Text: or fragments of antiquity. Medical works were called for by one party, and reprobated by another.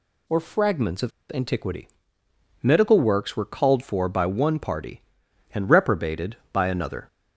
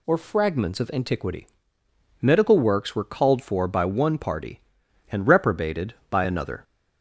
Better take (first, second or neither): second